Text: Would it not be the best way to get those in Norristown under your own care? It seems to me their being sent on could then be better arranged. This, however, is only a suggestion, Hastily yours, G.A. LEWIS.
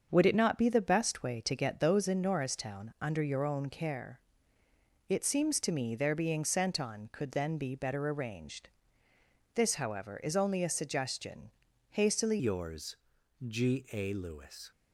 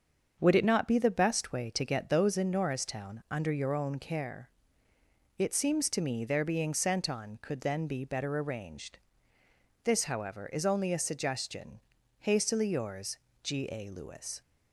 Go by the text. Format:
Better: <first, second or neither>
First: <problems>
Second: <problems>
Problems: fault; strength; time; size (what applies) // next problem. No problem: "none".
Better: second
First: starts louder than the rest; until 1.1 s; 7 dB // changes voice at "yours"; from 12.3 s on; 2.4 s long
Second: starts louder than the rest; until 1.4 s; 7 dB